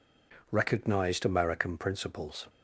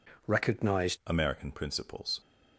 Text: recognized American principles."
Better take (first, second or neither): first